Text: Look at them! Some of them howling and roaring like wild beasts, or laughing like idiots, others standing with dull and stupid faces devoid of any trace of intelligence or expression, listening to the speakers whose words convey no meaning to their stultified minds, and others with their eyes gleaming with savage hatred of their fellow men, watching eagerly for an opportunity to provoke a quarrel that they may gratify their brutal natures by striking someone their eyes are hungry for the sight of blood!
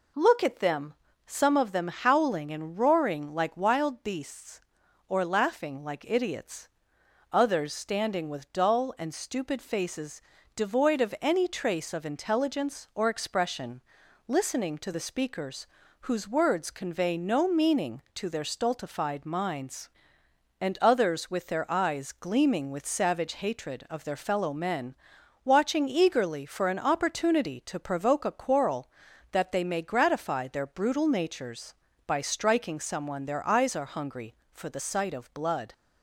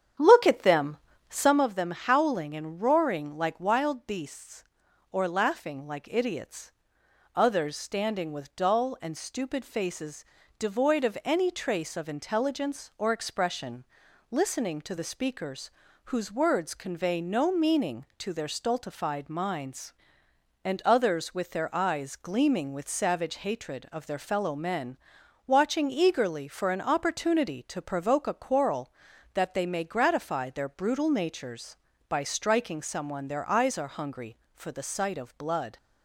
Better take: first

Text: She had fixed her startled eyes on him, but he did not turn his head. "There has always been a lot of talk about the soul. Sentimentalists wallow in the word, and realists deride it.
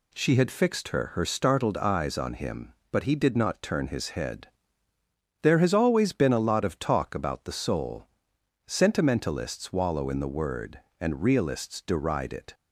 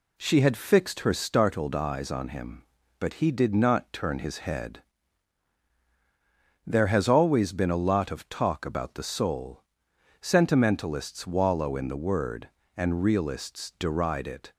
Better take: second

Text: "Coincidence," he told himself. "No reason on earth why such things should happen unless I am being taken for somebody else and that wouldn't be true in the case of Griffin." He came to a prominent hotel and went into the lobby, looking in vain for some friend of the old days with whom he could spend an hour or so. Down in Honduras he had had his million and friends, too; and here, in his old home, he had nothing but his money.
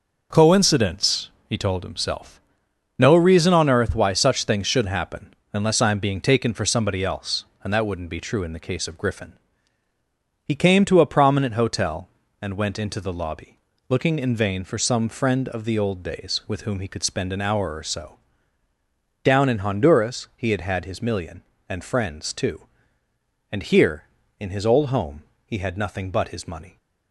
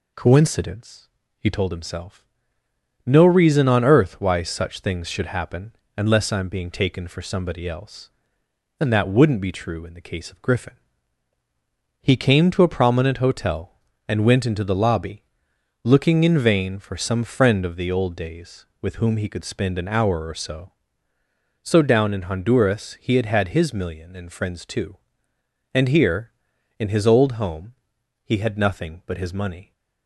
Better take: first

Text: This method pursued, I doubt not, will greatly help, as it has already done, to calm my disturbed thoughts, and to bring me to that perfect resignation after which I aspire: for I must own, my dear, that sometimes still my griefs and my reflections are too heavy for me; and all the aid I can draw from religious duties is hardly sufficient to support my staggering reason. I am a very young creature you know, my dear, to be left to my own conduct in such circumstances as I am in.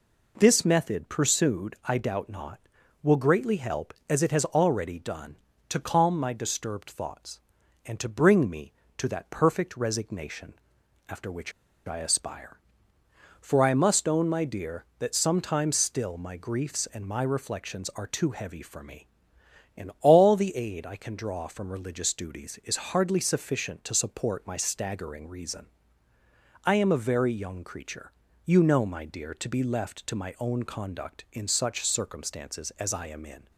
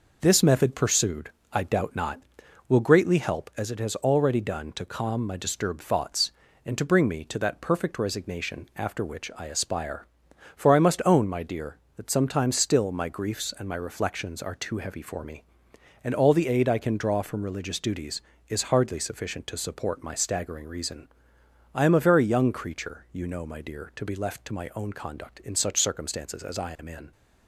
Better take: second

